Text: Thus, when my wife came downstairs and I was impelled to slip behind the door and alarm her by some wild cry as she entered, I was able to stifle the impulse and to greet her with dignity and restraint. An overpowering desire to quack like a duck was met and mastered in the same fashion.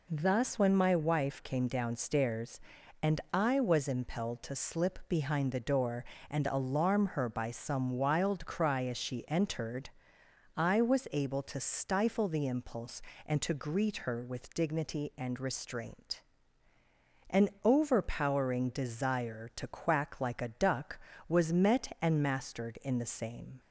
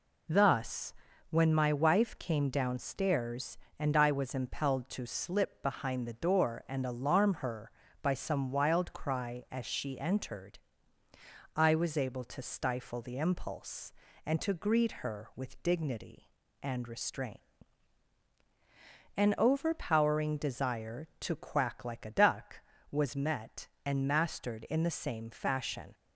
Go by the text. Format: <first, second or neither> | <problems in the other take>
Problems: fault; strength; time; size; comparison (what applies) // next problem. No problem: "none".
second | stops before "fashion"; at 23.5 s